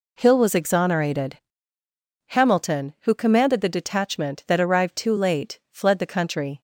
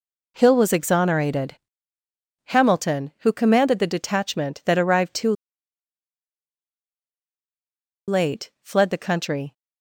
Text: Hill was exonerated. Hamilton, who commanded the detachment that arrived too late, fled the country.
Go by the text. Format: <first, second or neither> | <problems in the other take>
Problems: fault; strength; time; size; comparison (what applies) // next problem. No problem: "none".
first | pauses between "too" and "late"; strong; at 5.3 s; 2.7 s long